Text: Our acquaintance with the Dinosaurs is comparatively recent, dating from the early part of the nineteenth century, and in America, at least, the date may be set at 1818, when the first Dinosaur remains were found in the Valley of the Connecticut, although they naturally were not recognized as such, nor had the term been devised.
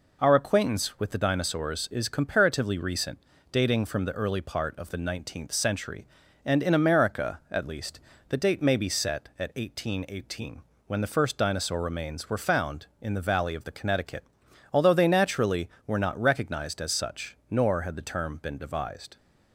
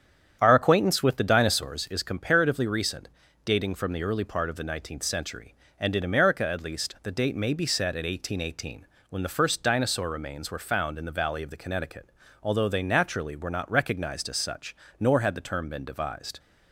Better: first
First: none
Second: starts louder than the rest; strong; until 1.8 s; 9 dB

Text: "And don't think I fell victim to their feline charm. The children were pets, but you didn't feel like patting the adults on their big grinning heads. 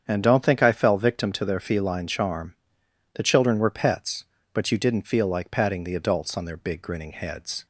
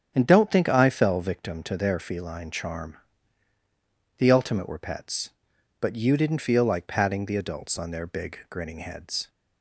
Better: first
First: starts louder than the rest; strong; until 1.0 s; 8 dB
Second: starts louder than the rest; strong; until 1.1 s; 8.5 dB // says "ultimate" for "children"; at 4.3 s

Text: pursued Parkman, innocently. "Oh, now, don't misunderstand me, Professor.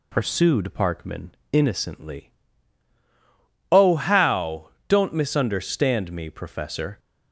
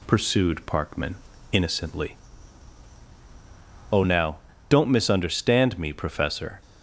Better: second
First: says "how" for "now"; at 3.9 s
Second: none

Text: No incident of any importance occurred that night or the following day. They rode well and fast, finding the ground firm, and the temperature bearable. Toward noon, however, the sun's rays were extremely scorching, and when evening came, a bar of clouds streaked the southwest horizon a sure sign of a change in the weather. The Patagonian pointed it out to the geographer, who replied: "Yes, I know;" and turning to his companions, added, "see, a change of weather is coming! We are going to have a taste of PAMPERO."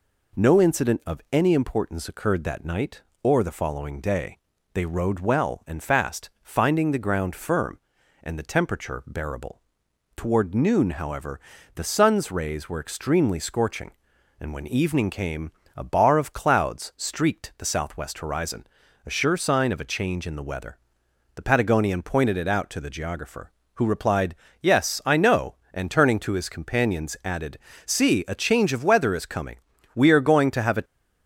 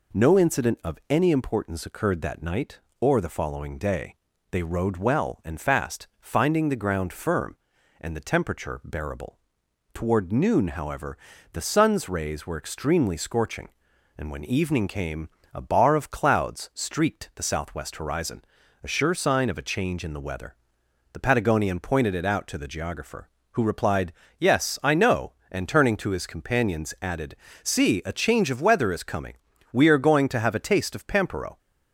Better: second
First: pauses between "horizon" and "a"; at 18.6 s; 0.40 s long // stops before "taste of PAMPERO"; at 30.8 s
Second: pauses between "horizon" and "a"; at 18.4 s; 0.40 s long

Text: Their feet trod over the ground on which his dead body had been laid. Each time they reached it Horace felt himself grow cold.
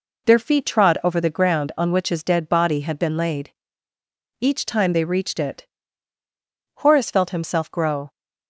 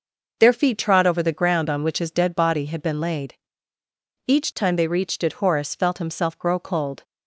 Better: second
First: pauses between "it" and "Horace"; at 5.6 s; 1.1 s long // stops before "cold"; at 8.1 s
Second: none

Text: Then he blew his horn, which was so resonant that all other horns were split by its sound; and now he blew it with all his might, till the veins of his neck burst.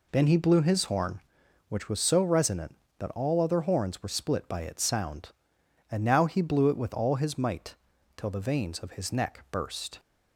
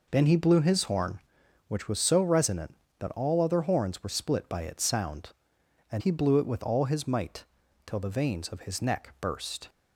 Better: first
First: none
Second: skips "now"; at 6.0 s

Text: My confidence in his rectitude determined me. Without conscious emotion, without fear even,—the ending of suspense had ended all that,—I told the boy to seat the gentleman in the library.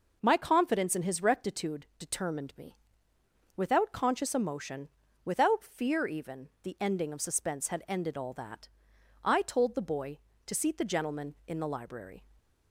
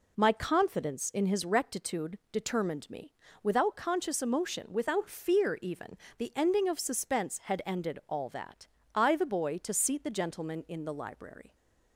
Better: first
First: none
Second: skips "told"; at 9.1 s

